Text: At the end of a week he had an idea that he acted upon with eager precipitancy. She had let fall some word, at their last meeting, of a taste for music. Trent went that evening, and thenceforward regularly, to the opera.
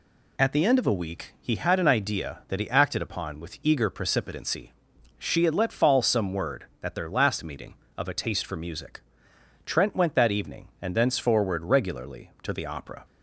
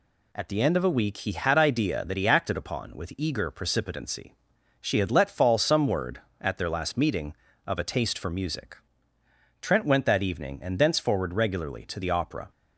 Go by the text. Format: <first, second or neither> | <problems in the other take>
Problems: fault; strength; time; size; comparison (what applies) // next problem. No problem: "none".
first | skips "an"; at 1.5 s